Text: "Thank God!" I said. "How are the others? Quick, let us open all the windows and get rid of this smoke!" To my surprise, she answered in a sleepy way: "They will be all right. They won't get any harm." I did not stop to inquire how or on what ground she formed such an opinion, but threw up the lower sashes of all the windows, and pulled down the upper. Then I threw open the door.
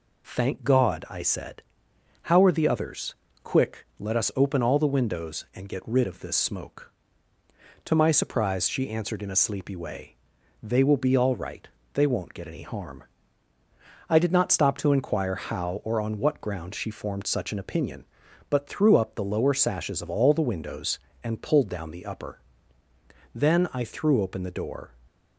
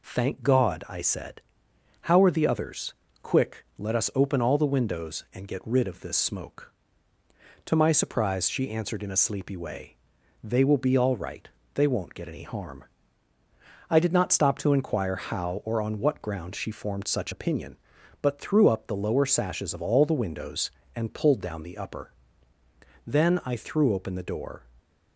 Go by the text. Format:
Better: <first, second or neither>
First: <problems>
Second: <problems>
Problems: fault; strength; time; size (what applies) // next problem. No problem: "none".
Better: first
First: none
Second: skips "an"; at 17.3 s